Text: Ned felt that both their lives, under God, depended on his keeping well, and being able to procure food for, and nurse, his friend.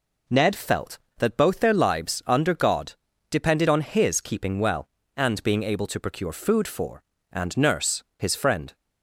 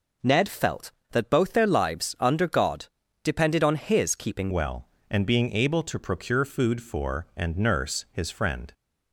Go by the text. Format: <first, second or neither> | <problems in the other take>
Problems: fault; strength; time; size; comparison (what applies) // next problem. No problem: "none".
first | changes voice at "well"; from 4.5 s on; 4.2 s long